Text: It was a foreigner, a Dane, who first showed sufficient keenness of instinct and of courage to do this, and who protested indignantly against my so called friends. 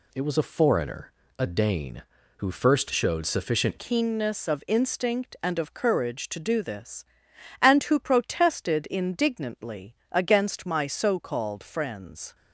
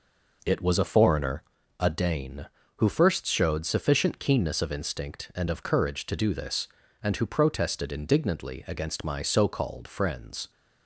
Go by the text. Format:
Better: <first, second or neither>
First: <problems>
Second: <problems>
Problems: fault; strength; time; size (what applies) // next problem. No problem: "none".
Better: second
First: changes voice at "keenness"; from 3.7 s on; 8.6 s long // pauses between "indignantly" and "against"; slight; at 9.9 s; 0.16 s long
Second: none